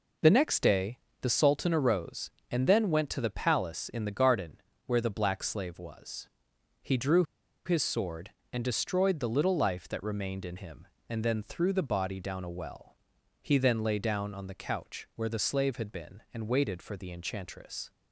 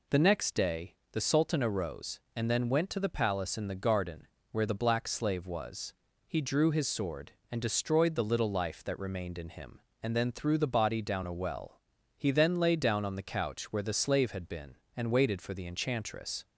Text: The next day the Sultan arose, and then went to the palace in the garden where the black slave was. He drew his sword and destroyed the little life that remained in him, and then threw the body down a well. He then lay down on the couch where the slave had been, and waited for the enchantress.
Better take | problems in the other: second | pauses between "day" and "the"; slight; at 0.9 s; 0.22 s long; slight in the second // pauses between "garden" and "where"; slight; at 4.6 s; 0.26 s long; slight in the second // pauses between "drew" and "his"; at 7.2 s; 0.42 s long

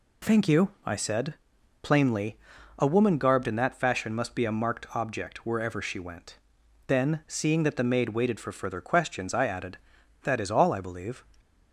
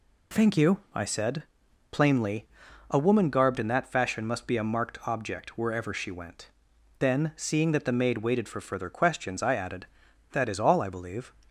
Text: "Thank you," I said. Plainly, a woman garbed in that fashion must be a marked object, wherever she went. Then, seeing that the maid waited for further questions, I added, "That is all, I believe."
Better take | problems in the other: neither | none

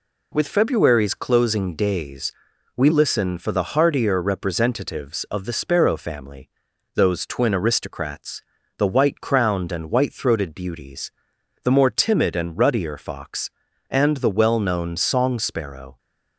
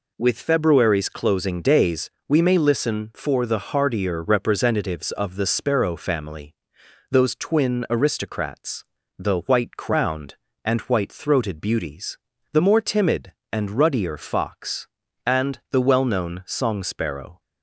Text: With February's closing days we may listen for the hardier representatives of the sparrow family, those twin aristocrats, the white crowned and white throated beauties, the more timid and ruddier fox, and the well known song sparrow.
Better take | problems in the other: second | pauses between "days" and "we"; at 2.3 s; 0.44 s long; slight in the second // skips "may"; at 2.8 s

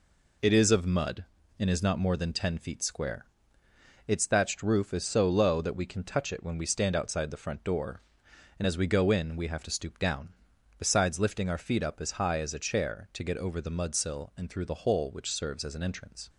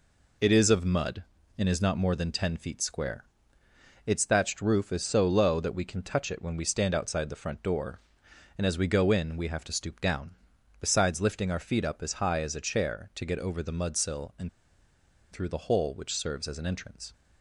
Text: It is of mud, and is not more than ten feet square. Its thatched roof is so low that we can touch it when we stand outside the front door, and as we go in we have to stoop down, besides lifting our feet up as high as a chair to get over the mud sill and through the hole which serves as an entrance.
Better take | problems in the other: first | pauses between "and" and "through"; noticeable; at 14.4 s; 0.84 s long

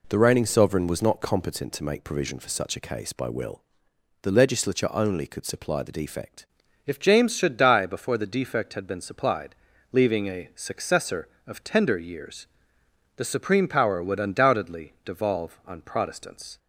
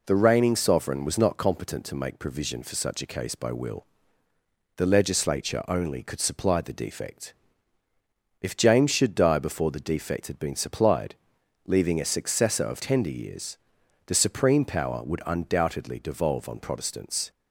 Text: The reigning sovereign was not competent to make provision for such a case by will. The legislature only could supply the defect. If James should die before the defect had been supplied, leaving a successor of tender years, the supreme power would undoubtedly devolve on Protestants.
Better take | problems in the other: second | changes voice at "If"; from 6.8 s on; 9.7 s long

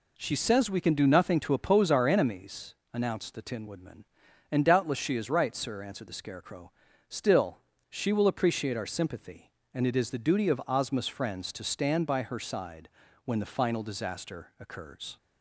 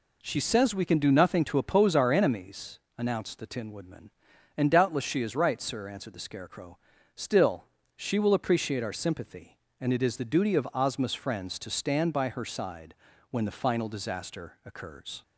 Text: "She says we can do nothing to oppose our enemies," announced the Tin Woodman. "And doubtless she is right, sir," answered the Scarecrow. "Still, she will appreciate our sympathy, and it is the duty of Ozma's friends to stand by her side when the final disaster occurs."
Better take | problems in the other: neither | pauses between "side" and "when"; slight; the same in both

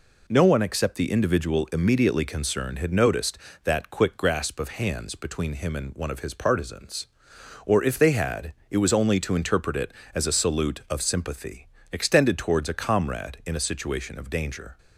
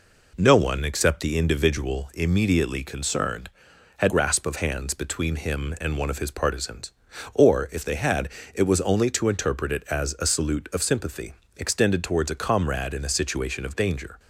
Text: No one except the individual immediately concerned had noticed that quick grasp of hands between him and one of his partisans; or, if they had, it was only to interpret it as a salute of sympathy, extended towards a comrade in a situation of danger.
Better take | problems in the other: first | skips "noticed that quick"; at 4.1 s

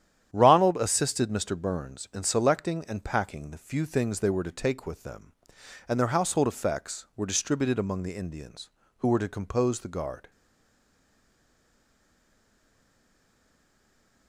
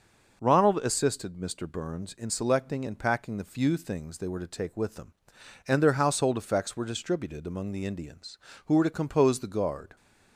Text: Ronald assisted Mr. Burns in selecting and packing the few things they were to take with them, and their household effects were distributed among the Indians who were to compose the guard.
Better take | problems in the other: second | starts louder than the rest; strong; until 1.3 s; 10 dB // stays silent after the last word; strong; from 10.3 s on; 3.9 s long

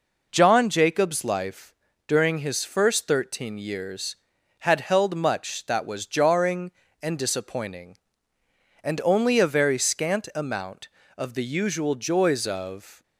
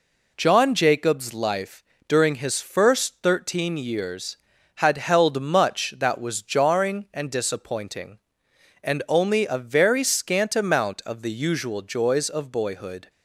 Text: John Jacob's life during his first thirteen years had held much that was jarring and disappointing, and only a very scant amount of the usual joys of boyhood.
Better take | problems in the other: second | pauses between "life" and "during"; slight; at 1.7 s; 0.32 s long; slight in the second // stops before "boyhood"; at 13.0 s

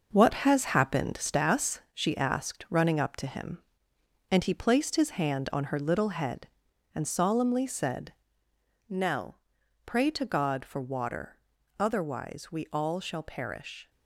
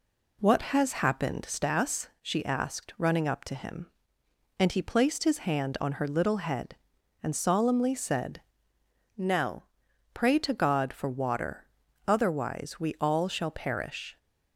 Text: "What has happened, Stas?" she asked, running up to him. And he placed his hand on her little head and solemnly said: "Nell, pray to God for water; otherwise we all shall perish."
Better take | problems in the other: second | gets quieter; strong; throughout; 7.5 dB

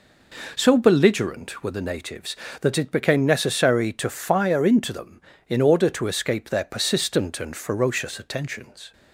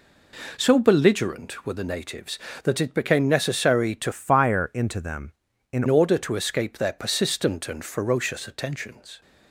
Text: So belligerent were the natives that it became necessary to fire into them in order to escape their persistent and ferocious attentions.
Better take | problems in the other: first | changes voice from "fire" to "in"; from 4.1 to 5.8 s; 1.7 s long

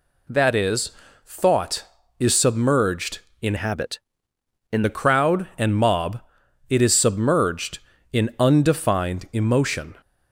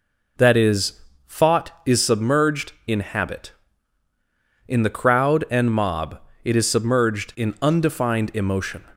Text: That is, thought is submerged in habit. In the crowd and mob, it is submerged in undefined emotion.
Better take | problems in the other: second | changes voice from "habit" to "In"; from 3.5 to 4.8 s; 1.3 s long

